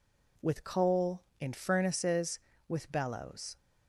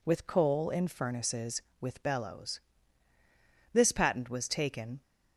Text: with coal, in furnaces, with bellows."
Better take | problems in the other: first | goes on to say "This patent was taken"; noticeable; from 3.7 s on; 1.3 s long

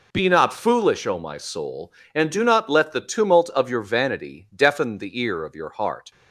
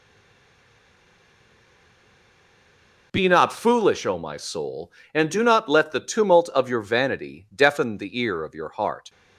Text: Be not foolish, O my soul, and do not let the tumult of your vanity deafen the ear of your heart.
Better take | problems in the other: first | stays silent before the first word; strong; until 3.1 s; 3.1 s long

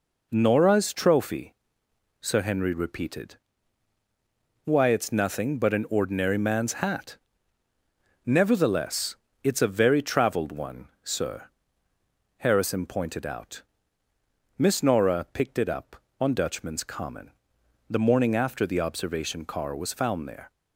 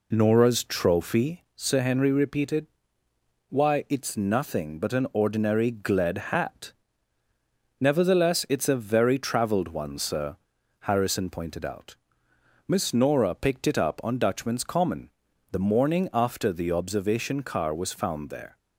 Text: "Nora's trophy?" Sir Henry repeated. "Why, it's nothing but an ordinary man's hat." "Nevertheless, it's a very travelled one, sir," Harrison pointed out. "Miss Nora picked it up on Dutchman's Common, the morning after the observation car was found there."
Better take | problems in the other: first | says "gled" for "man's"; at 5.7 s

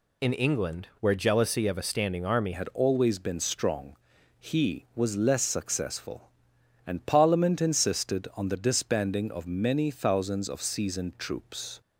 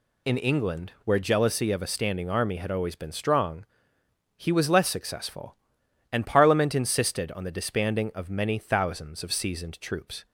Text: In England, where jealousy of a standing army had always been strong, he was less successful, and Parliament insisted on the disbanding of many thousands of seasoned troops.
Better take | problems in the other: second | changes voice at "had"; from 2.5 s on; 9.3 s long

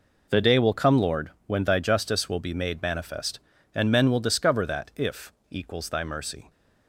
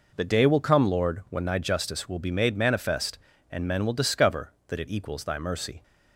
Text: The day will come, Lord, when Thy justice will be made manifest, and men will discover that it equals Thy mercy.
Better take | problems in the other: second | says "if" for "it"; at 4.9 s

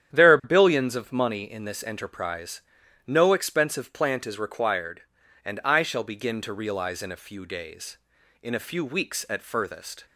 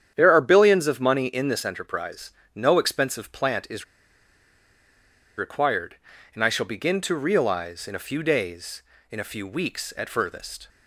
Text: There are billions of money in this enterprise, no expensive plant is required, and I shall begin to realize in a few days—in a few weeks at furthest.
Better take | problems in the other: first | starts louder than the rest; strong; until 1.1 s; 9 dB; strong in the first // pauses between "is" and "required"; strong; at 3.8 s; 1.5 s long

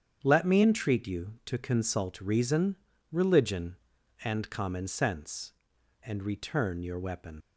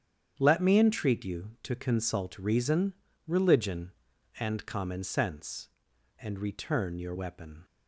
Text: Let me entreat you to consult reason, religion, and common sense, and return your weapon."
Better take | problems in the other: second | starts louder than the rest; strong; until 1.2 s; 8.5 dB; strong in the second // leaves "weapon" unfinished; at 7.4 s; 95 ms

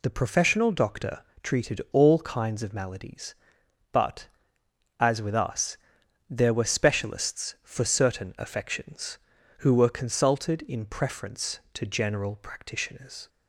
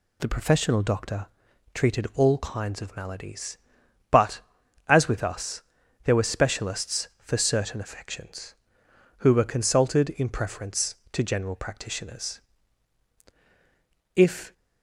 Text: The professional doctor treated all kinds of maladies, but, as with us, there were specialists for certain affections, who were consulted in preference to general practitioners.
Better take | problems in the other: first | pauses between "doctor" and "treated"; noticeable; at 1.2 s; 0.48 s long; slight in the first // goes on to say "If"; slight; from 14.1 s on; 0.38 s long

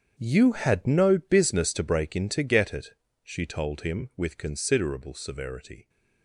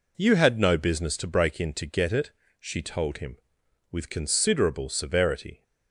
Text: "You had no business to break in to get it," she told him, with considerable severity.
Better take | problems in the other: second | gets quieter; strong; throughout; 13.5 dB

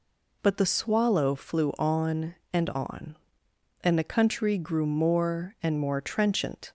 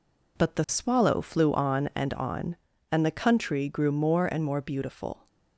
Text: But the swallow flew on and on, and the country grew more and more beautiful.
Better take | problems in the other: second | says "trenchant" for "beautiful"; at 5.9 s

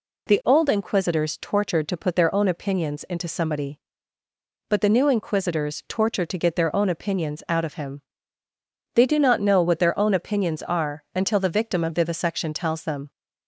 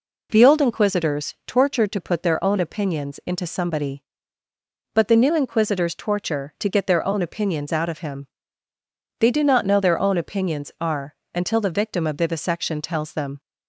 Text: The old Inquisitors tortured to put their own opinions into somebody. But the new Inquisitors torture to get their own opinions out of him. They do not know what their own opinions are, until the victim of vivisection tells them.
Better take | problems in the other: first | skips "what"; at 9.7 s

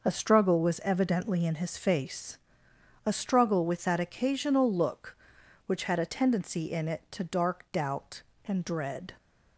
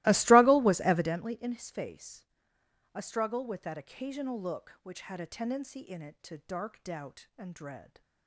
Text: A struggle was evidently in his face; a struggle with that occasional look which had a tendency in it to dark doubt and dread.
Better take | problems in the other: first | starts louder than the rest; strong; until 1.2 s; 19 dB

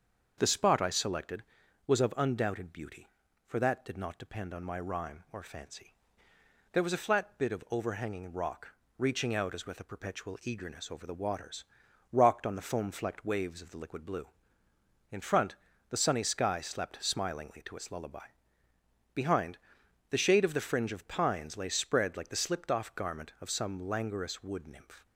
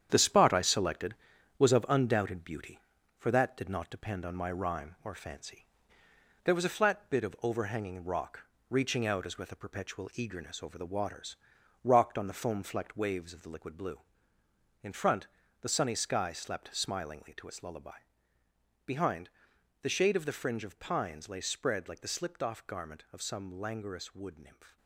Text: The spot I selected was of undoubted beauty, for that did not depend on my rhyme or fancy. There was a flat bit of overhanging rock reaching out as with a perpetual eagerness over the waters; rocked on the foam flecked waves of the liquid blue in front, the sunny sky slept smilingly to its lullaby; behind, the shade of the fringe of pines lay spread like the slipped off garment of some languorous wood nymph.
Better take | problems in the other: first | gets quieter; throughout; 7 dB // starts louder than the rest; strong; until 1.1 s; 9 dB; also in the first // pauses between "rock" and "reaching"; slight; at 8.4 s; 0.28 s long; slight in the first

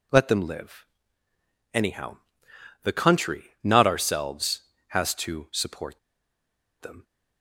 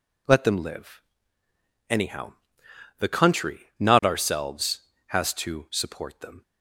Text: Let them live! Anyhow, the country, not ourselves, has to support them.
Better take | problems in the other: second | pauses between "support" and "them"; noticeable; at 5.9 s; 0.82 s long

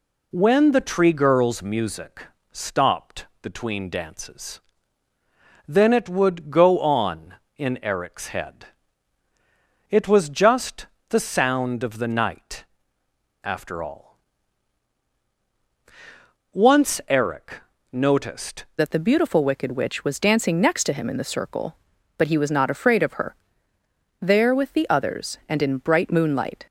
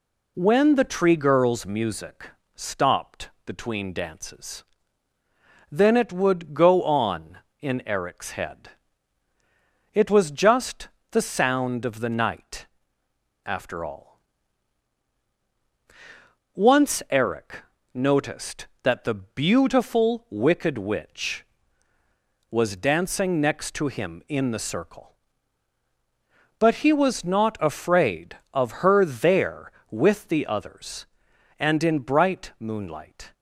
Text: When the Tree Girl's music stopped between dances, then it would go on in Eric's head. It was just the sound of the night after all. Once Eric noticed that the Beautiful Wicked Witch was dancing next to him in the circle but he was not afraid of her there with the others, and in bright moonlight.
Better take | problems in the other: second | pauses between "music" and "stopped"; slight; at 2.2 s; 0.26 s long; slight in the second // pauses between "stopped" and "between"; slight; at 3.2 s; 0.16 s long; slight in the second // pauses between "just" and "the"; slight; at 10.8 s; 0.24 s long; slight in the second // pauses between "night" and "after"; noticeable; at 12.6 s; 0.80 s long; noticeable in the second // pauses between "Eric" and "noticed"; slight; at 17.5 s; 0.36 s long; slight in the second // changes voice at "that"; from 18.7 s on; 7.9 s long // pauses between "her" and "there"; noticeable; at 23.3 s; 0.84 s long

